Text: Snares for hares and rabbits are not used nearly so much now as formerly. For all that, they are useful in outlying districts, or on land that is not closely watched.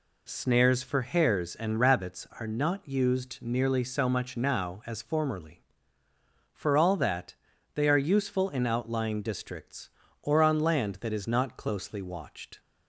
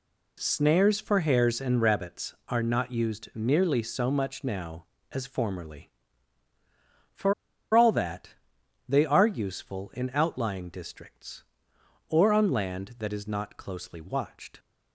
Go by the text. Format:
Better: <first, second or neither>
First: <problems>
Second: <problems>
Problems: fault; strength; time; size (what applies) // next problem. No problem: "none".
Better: first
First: none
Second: pauses between "For" and "all"; at 7.3 s; 0.41 s long